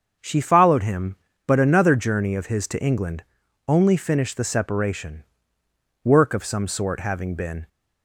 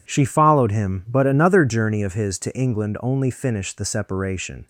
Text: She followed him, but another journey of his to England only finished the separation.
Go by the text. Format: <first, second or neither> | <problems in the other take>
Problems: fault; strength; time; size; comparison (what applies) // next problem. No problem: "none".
second | starts louder than the rest; until 1.4 s; 6.5 dB // pauses between "England" and "only"; at 3.2 s; 0.42 s long // goes on to say "Work of some sort having been"; from 6.0 s on; 1.6 s long